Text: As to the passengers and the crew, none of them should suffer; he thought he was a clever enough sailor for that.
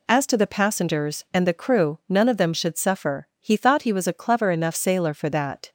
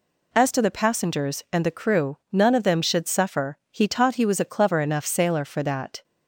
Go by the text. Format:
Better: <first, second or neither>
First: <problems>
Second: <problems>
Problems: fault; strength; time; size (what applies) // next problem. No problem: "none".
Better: first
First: none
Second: says "taught" for "thought"; at 3.8 s